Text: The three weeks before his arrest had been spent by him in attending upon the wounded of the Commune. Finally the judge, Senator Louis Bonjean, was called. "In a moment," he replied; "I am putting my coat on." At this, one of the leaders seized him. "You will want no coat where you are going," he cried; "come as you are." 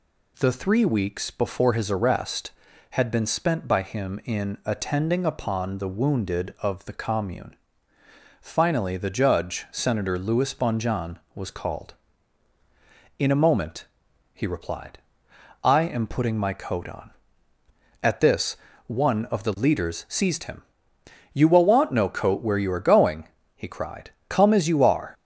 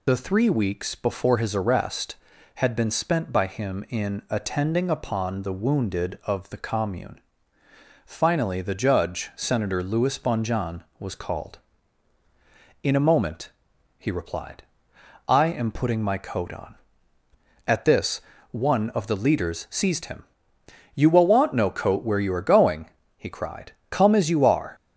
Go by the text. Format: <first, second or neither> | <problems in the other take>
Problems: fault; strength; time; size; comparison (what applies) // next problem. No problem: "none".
first | loses the start of "The"; at 0.0 s; 65 ms